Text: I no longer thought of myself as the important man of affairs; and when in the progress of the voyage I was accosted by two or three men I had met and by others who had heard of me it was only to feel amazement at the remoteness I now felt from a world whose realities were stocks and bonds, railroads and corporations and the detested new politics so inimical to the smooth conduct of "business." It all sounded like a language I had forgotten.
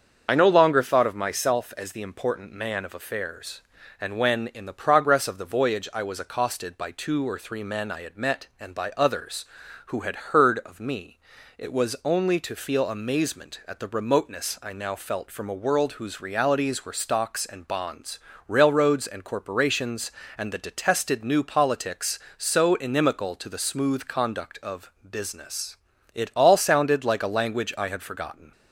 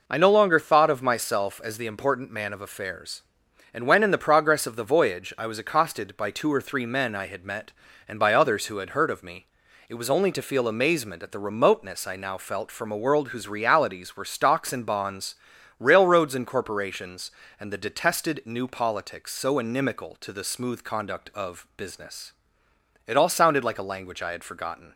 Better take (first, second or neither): second